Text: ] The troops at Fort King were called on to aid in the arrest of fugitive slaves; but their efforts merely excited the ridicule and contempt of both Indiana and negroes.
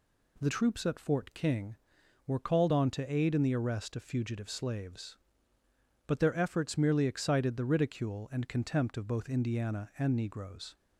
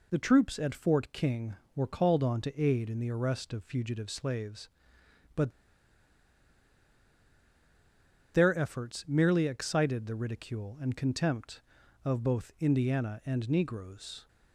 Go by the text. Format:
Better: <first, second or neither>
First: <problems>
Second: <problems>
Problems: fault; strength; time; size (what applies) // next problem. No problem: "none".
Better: first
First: none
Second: pauses between "but" and "their"; strong; at 5.4 s; 2.8 s long